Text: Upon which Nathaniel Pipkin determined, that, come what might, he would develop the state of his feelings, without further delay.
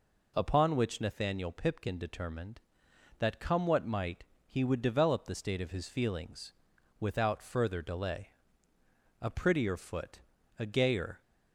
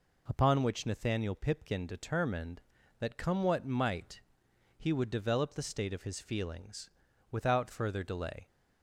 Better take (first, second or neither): second